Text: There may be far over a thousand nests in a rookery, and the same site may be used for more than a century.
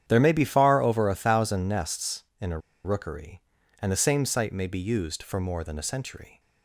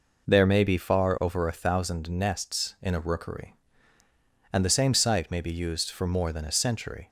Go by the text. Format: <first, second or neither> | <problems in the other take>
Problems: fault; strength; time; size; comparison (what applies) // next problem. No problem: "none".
second | starts louder than the rest; strong; until 1.0 s; 9.5 dB // pauses between "a" and "rookery"; slight; at 2.5 s; 0.26 s long